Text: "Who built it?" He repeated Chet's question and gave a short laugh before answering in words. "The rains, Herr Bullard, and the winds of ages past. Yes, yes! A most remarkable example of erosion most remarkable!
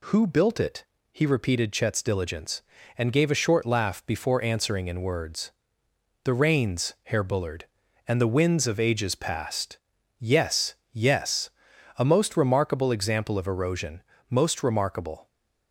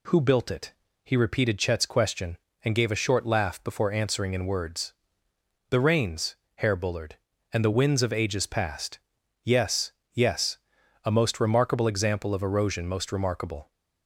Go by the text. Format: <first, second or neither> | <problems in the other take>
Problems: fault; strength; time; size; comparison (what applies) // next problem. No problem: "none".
second | says "diligence" for "question"; at 2.0 s // pauses between "erosion" and "most"; slight; at 14.0 s; 0.30 s long